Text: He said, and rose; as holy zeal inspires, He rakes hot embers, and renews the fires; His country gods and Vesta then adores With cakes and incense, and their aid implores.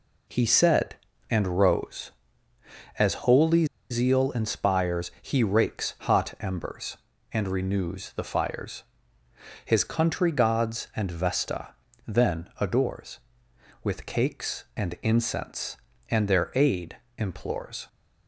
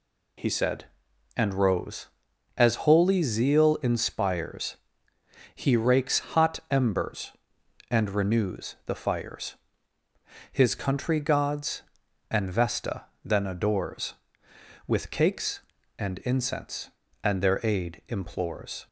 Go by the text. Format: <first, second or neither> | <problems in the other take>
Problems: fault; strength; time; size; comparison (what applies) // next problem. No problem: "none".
second | pauses between "holy" and "zeal"; slight; at 3.6 s; 0.25 s long // pauses between "Vesta" and "then"; slight; at 11.6 s; 0.36 s long; slight in the second // pauses between "aid" and "implores"; slight; at 16.9 s; 0.20 s long